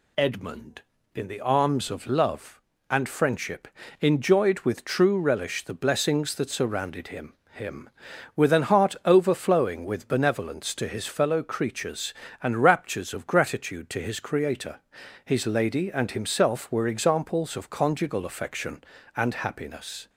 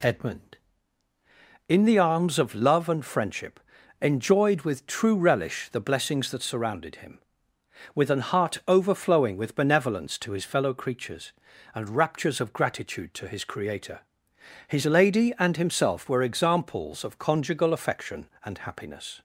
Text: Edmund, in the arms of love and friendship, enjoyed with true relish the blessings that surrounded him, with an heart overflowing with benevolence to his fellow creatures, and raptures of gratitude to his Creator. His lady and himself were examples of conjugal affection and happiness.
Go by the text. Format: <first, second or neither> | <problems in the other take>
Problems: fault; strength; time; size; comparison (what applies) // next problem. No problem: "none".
second | says "him" twice; at 7.5 s